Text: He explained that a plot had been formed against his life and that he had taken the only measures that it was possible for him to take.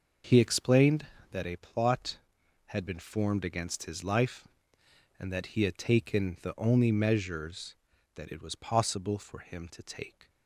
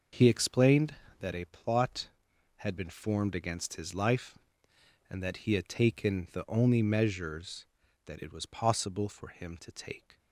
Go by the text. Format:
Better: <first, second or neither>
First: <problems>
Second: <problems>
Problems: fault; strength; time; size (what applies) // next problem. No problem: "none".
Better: neither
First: none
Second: none